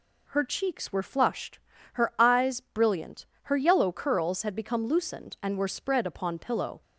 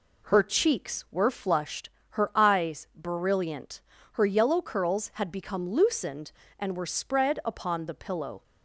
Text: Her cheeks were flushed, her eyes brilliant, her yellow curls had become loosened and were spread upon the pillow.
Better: second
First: skips "the"; at 6.3 s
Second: none

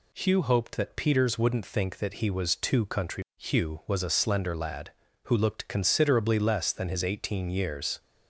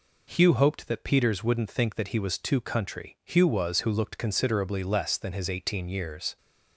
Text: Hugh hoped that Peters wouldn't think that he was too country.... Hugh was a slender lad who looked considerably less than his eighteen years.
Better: first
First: none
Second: skips "a slender lad"; at 3.8 s

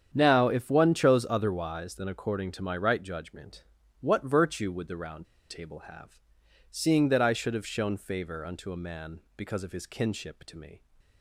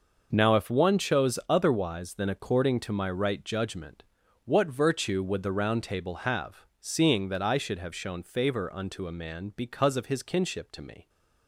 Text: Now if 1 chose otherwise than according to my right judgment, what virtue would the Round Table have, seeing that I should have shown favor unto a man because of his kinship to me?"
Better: second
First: starts louder than the rest; strong; until 1.1 s; 8.5 dB // pauses between "Round" and "Table"; slight; at 5.2 s; 0.24 s long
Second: none

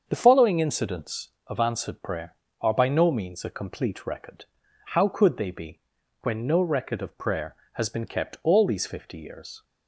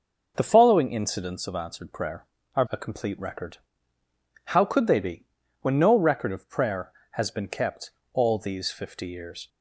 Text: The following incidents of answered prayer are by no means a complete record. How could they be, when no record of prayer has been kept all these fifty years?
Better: first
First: starts louder than the rest; until 1.0 s; 7 dB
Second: starts louder than the rest; noticeable; until 1.3 s; 6 dB // skips "by no means"; at 2.6 s // pauses between "kept" and "all"; slight; at 7.8 s; 0.24 s long

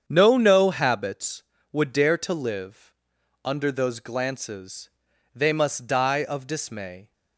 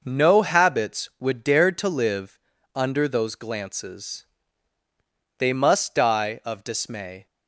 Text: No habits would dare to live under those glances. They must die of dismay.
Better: second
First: starts louder than the rest; strong; until 1.0 s; 8 dB // says "No" twice; at 0.3 s // pauses between "live" and "under"; noticeable; at 2.9 s; 0.52 s long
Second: pauses between "live" and "under"; slight; at 2.3 s; 0.34 s long

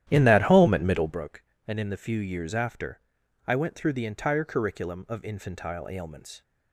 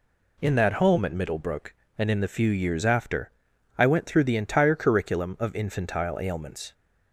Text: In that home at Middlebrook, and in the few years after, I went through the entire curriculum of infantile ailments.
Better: second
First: starts louder than the rest; strong; until 1.2 s; 11.5 dB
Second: none

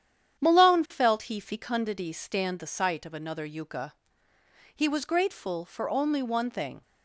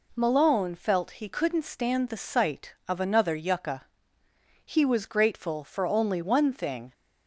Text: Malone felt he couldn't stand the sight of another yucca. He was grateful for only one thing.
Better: second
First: starts louder than the rest; strong; until 1.4 s; 9 dB // says "fecundity" for "couldn't"; at 1.3 s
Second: none

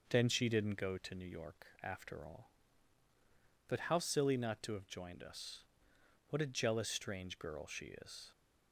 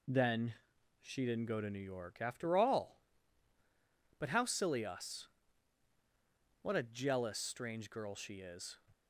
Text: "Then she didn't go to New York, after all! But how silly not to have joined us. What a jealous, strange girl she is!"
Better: first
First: none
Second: pauses between "Then" and "she"; noticeable; at 0.5 s; 0.46 s long // skips "not to have joined"; at 4.8 s

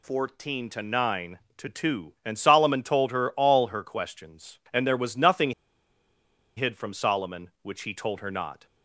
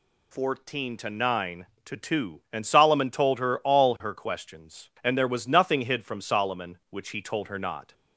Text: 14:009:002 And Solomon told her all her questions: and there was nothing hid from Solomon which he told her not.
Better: second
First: pauses between "nothing" and "hid"; at 5.5 s; 1.0 s long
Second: none

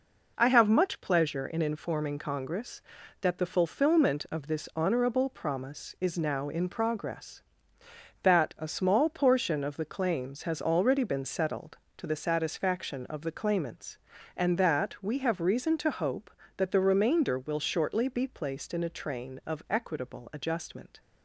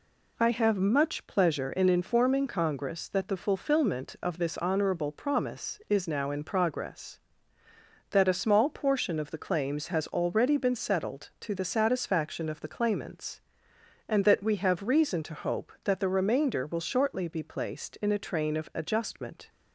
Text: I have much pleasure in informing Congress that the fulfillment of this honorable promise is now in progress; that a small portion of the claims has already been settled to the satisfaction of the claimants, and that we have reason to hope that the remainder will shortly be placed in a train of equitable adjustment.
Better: first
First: none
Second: skips "equitable"; at 18.7 s

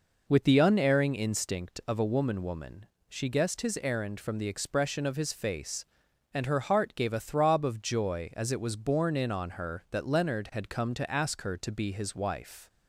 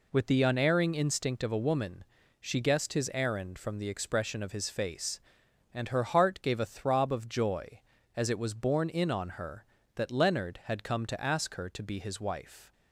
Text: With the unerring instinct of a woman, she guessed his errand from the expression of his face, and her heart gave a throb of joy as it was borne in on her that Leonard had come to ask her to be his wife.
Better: second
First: says "woman" twice; at 2.4 s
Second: none

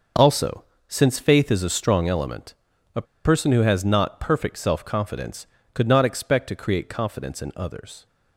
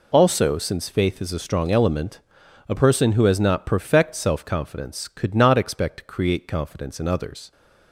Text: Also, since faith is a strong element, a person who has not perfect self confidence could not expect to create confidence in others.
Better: second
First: starts louder than the rest; noticeable; until 1.4 s; 6 dB // pauses between "a" and "person"; slight; at 3.0 s; 0.21 s long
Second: none

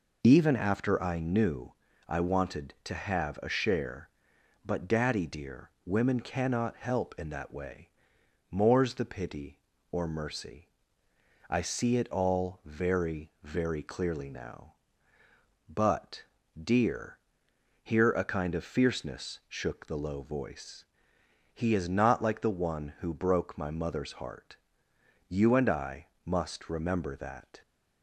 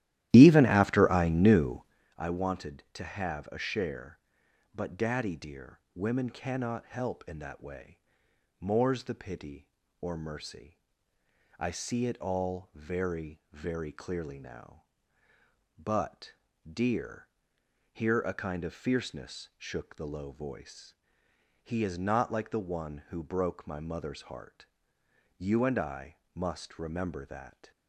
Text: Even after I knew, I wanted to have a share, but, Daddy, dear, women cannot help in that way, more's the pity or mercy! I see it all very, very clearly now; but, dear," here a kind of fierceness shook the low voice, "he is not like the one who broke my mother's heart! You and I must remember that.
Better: first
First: pauses between "I" and "must"; slight; at 26.0 s; 0.16 s long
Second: starts louder than the rest; strong; until 2.1 s; 13.5 dB // pauses between "I" and "must"; slight; at 26.1 s; 0.16 s long

